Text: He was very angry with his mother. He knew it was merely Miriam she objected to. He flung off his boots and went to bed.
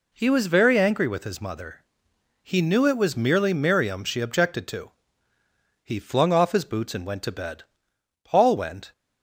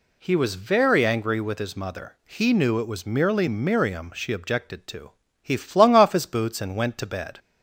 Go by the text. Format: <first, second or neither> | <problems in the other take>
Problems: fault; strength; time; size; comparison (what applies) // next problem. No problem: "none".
second | goes on to say "Paul went"; noticeable; from 8.2 s on; 0.68 s long